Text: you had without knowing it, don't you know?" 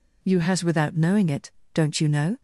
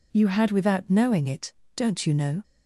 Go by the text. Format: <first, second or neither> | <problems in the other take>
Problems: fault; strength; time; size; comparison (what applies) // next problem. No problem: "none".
second | says "has" for "had"; at 0.4 s